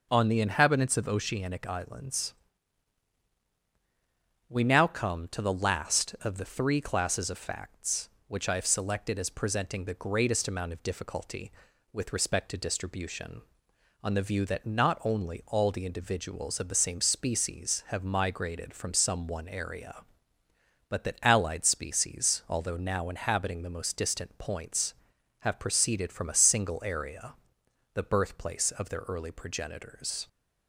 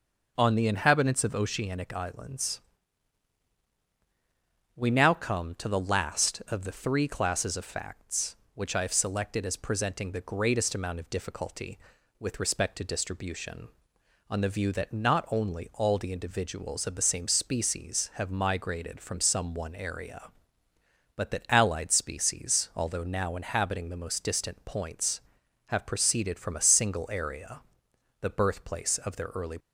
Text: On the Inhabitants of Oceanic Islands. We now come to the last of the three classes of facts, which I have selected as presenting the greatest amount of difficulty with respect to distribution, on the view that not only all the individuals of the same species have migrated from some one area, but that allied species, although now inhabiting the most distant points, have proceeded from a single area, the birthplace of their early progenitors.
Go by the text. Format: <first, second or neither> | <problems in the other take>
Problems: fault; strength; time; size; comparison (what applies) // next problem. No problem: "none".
first | stops before "progenitors"; at 29.5 s